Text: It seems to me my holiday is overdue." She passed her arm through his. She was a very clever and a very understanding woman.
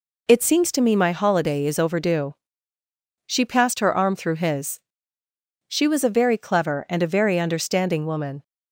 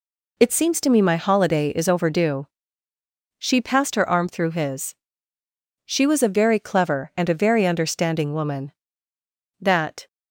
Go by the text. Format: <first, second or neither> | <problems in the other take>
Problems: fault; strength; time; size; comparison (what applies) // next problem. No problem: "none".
first | goes on to say "That"; slight; from 9.6 s on; 0.46 s long